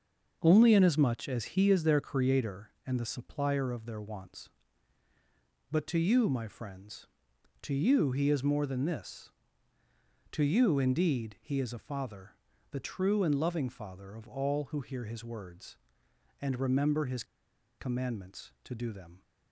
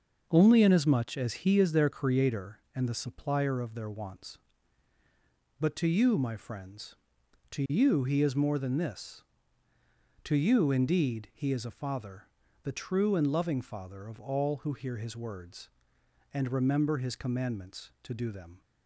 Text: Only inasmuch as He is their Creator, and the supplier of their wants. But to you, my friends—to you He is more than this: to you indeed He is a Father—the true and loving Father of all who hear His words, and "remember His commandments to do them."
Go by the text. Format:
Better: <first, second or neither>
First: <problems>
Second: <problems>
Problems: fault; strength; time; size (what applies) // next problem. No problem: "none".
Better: second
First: starts louder than the rest; noticeable; until 1.4 s; 6 dB // pauses between "His" and "commandments"; noticeable; at 17.2 s; 0.55 s long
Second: starts louder than the rest; noticeable; until 1.3 s; 6 dB